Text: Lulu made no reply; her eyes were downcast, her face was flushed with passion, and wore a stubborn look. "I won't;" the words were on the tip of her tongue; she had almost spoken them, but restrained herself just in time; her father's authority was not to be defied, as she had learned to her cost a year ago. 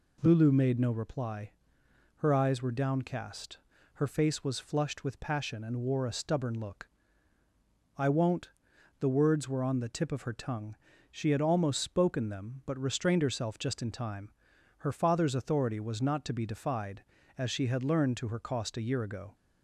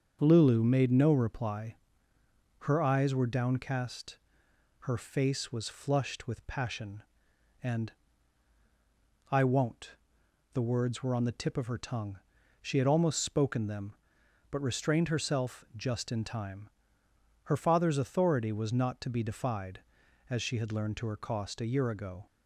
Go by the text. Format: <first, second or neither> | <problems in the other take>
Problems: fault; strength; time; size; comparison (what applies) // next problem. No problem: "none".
first | starts louder than the rest; strong; until 1.2 s; 7 dB // skips "wore a stubborn look"; at 8.6 s